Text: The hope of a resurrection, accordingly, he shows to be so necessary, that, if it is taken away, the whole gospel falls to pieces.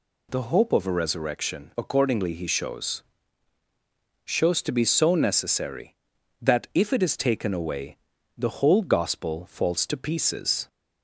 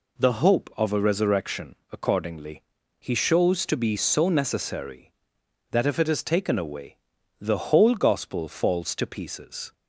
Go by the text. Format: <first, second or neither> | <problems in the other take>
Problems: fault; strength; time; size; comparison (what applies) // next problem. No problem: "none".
second | says "shows" twice; at 4.2 s